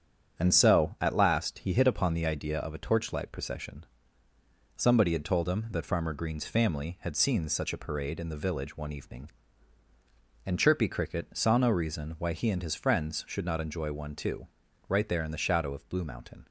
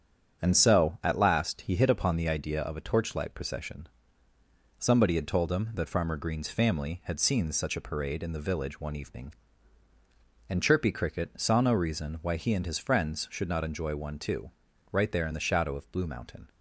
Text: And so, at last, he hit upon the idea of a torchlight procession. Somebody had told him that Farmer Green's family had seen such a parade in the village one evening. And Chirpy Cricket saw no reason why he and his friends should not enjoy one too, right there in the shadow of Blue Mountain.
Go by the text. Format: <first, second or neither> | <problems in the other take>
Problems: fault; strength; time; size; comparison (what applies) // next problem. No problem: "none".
neither | starts louder than the rest; strong; the same in both